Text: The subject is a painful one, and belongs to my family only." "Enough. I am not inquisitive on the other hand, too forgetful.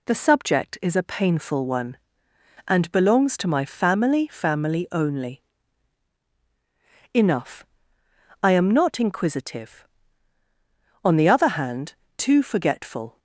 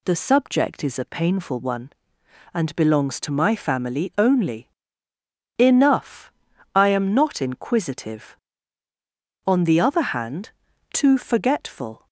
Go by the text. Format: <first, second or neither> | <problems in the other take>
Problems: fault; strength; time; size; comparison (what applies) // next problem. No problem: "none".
second | says "family" twice; at 4.2 s